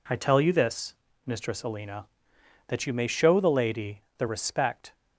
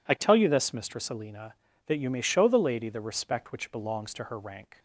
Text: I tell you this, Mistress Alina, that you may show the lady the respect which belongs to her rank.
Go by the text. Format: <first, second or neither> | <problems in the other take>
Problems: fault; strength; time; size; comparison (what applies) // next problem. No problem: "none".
second | pauses between "lady" and "the"; slight; at 4.0 s; 0.16 s long // stops before "which belongs to her rank"; at 4.9 s